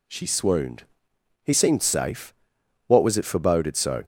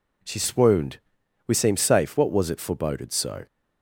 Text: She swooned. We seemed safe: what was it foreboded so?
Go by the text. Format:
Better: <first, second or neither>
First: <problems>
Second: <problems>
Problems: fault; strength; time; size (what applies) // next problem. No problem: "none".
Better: second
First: says "He" for "We"; at 1.4 s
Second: none